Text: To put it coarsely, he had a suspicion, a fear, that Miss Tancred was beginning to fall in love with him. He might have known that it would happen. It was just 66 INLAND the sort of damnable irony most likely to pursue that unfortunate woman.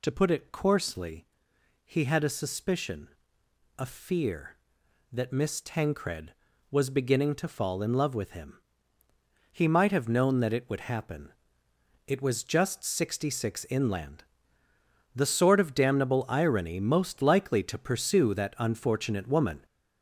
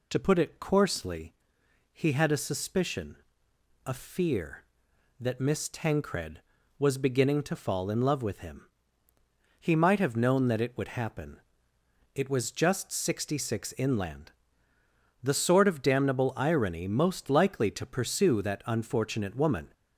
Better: second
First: gets louder; noticeable; throughout; 5.5 dB // pauses between "INLAND" and "the"; noticeable; at 14.2 s; 0.92 s long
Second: pauses between "INLAND" and "the"; noticeable; at 14.3 s; 0.92 s long

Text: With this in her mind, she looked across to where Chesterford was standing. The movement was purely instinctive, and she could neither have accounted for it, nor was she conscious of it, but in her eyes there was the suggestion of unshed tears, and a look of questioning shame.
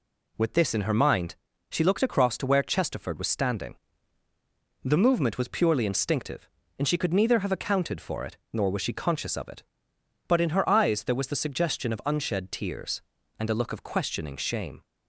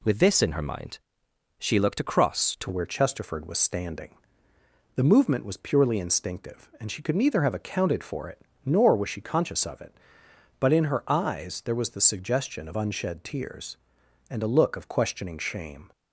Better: first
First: none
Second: changes voice at "where"; from 2.7 s on; 13.2 s long

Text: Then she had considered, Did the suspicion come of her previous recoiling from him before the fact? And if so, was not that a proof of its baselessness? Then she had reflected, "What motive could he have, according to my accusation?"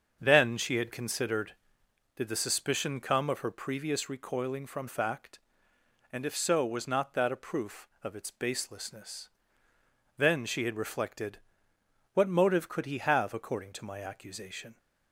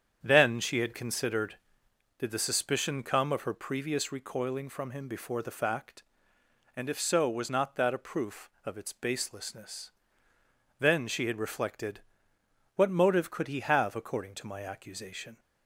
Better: second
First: starts louder than the rest; until 1.2 s; 6.5 dB // skips "him before the"; at 4.8 s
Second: starts louder than the rest; strong; until 1.2 s; 8 dB

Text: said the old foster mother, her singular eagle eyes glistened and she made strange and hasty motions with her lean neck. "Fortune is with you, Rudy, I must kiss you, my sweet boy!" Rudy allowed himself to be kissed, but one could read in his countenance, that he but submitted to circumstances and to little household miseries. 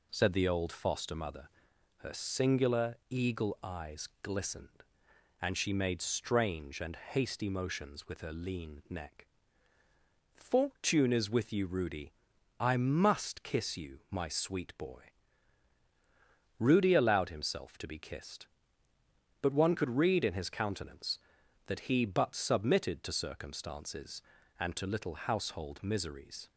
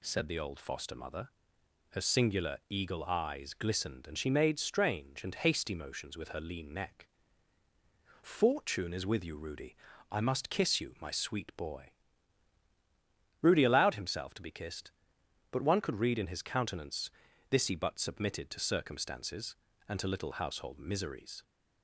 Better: first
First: none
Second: says "this" for "that"; at 17.4 s

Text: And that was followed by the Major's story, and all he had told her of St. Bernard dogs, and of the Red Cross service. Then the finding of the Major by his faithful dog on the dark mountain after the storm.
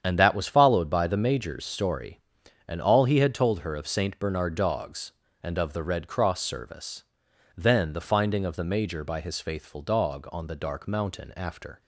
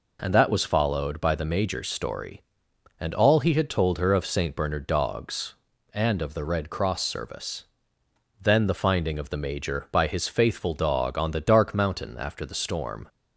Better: second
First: starts louder than the rest; strong; until 1.0 s; 8.5 dB // stops before "the storm"; at 11.8 s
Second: none

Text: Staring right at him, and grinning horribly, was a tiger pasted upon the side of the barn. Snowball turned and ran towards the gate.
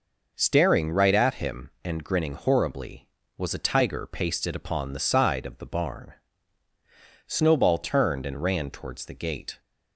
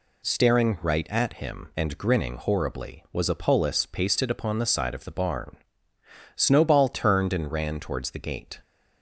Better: first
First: none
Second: says "polis" for "tiger"; at 3.3 s

